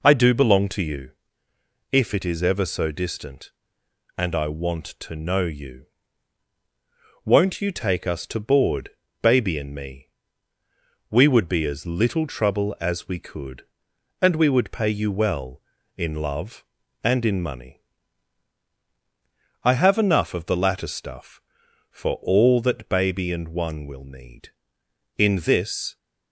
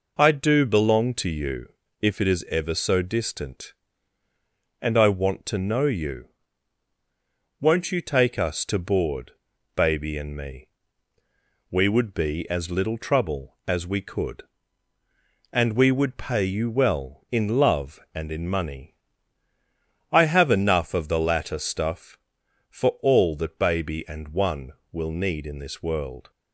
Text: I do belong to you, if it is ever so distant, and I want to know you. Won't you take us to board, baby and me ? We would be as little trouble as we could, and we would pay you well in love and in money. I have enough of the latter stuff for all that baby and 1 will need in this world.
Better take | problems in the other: second | stops before "world"; at 25.9 s

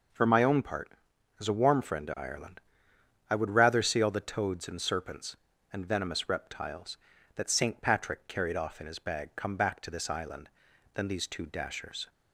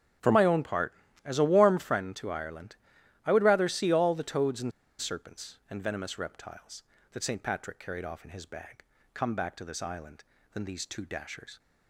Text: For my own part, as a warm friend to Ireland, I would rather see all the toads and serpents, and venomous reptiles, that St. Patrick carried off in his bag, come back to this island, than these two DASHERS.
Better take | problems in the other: first | starts louder than the rest; strong; until 1.5 s; 9.5 dB // pauses between "and" and "serpents"; slight; at 4.7 s; 0.28 s long

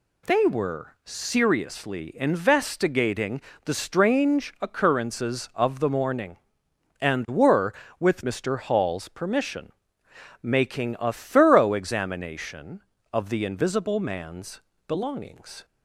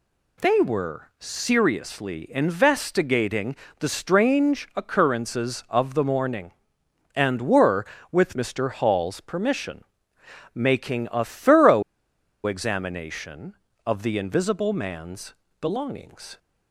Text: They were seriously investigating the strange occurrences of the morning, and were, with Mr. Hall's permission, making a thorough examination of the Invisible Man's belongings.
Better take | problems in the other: first | pauses between "investigating" and "the"; slight; at 3.5 s; 0.24 s long; slight in the first // pauses between "thorough" and "examination"; noticeable; at 11.8 s; 0.63 s long // pauses between "Man's" and "belongings"; slight; at 15.3 s; 0.26 s long; slight in the first

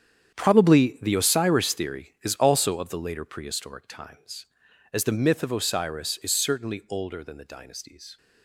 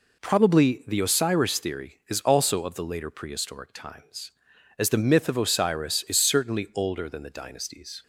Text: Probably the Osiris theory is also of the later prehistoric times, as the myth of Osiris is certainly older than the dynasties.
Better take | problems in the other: second | gets quieter; strong; throughout; 12.5 dB

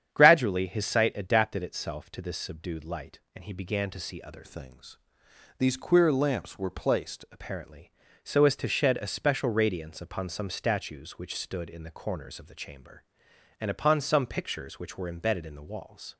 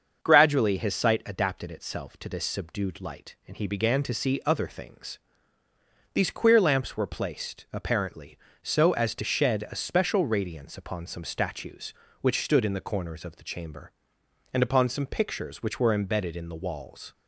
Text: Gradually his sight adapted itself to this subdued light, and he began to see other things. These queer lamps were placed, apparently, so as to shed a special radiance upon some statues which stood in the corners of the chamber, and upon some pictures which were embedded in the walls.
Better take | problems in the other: second | starts louder than the rest; strong; until 1.1 s; 9 dB; also in the second // changes voice from "things" to "placed"; from 4.4 to 7.2 s; 2.8 s long

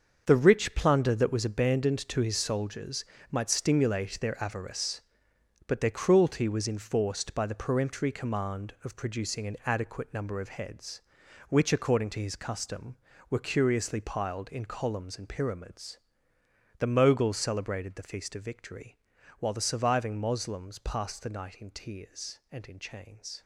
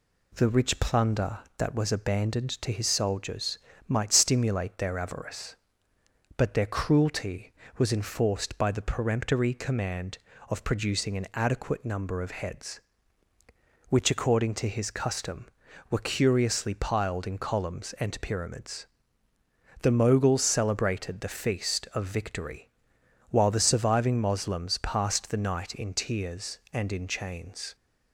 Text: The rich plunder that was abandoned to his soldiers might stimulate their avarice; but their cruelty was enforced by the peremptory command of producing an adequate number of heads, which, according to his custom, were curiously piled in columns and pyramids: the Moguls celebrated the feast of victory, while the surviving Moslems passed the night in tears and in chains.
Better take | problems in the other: second | gets quieter; strong; throughout; 10.5 dB // pauses between "soldiers" and "might"; slight; at 3.0 s; 0.28 s long; slight in the second

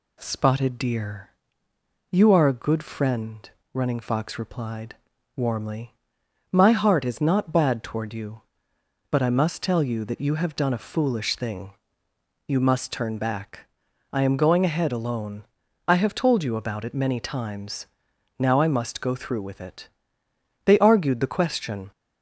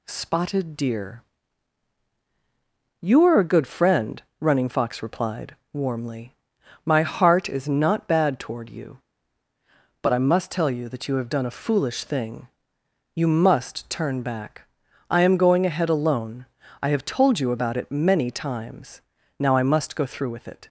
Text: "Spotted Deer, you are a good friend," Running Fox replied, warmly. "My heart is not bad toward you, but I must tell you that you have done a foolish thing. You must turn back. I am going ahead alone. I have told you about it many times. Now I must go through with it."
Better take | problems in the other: second | goes on to say "They argued the question"; noticeable; from 20.6 s on; 1.2 s long

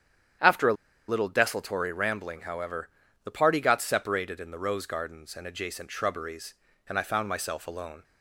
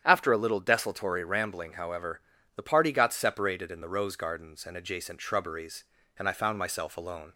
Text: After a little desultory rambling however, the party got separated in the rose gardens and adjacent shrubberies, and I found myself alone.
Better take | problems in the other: second | starts louder than the rest; strong; until 1.7 s; 9 dB; strong in the second // pauses between "a" and "little"; slight; at 0.7 s; 0.35 s long

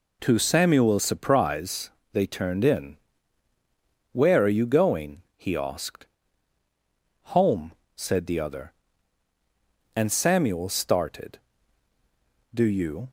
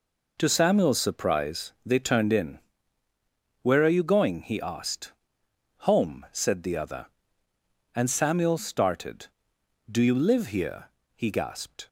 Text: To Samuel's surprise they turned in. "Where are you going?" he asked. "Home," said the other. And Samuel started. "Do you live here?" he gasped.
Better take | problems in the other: second | pauses between "surprise" and "they"; slight; at 1.8 s; 0.22 s long // stops before "live here he gasped"; at 13.0 s

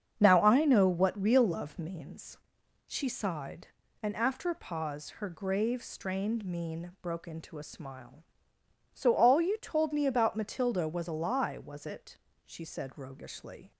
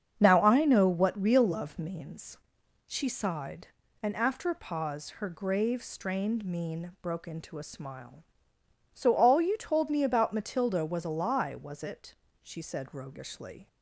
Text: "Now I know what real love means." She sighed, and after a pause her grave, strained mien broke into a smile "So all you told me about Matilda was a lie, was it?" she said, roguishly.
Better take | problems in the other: neither | starts louder than the rest; strong; the same in both

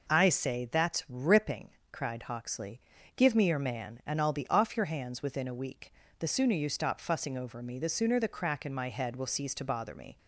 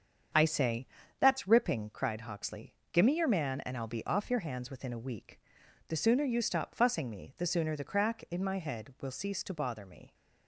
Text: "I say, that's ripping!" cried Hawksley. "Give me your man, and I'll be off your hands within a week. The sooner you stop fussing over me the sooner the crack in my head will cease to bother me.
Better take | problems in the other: first | starts louder than the rest; strong; until 1.6 s; 7 dB // skips "over"; at 7.0 s

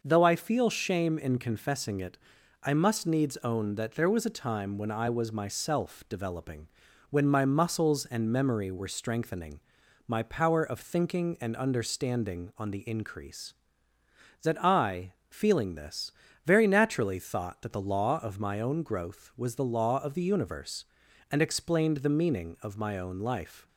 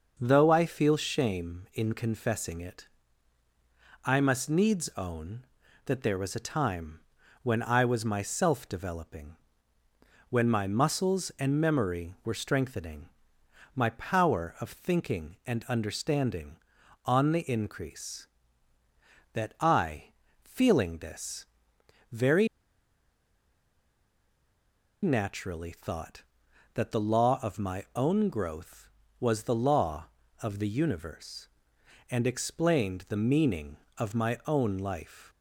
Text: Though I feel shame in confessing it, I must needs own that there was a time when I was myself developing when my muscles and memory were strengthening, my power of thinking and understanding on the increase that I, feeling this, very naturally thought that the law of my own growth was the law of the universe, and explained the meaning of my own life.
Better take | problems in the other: first | starts louder than the rest; noticeable; until 1.2 s; 6 dB // pauses between "time" and "when"; noticeable; at 6.9 s; 0.46 s long // pauses between "developing" and "when"; noticeable; at 9.3 s; 0.94 s long; also in the first // pauses between "very" and "naturally"; strong; at 22.4 s; 2.5 s long

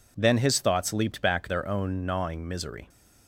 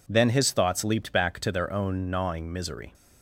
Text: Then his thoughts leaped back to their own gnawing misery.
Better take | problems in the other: second | skips "to"; at 1.4 s

